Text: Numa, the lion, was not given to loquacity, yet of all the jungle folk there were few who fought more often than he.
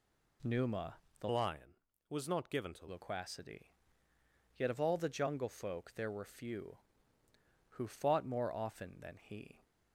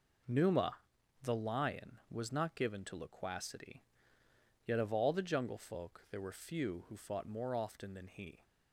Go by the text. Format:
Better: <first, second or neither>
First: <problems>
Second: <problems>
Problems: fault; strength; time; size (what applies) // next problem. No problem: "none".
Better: second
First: changes voice from "lion" to "to"; from 1.2 to 2.8 s; 1.6 s long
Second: none